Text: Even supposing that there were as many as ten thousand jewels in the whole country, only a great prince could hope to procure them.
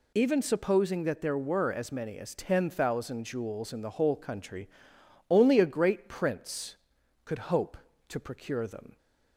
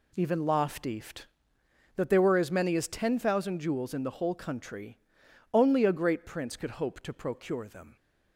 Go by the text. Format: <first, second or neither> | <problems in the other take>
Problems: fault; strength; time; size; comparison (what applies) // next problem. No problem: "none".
first | says "loftieft" for "supposing"; at 0.3 s